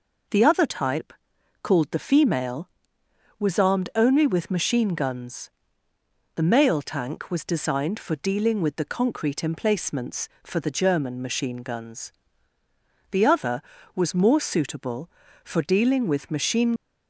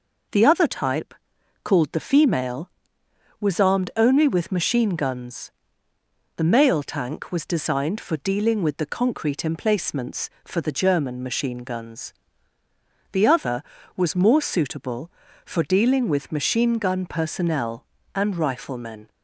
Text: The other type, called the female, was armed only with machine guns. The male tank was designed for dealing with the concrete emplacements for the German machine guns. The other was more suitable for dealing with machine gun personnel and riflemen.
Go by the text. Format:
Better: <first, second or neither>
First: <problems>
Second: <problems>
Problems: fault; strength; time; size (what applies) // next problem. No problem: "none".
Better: second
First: stops before "gun personnel and riflemen"; at 16.7 s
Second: none